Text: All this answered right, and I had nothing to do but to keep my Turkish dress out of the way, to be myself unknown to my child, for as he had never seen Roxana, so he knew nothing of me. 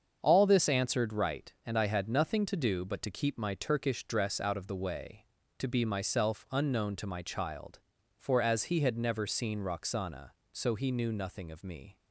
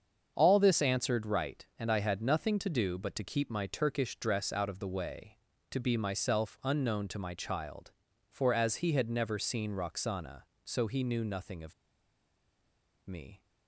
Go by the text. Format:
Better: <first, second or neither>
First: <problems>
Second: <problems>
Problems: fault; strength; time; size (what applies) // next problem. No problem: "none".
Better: first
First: starts louder than the rest; until 1.2 s; 7 dB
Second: starts louder than the rest; until 1.3 s; 7 dB // pauses between "of" and "me"; strong; at 11.7 s; 1.3 s long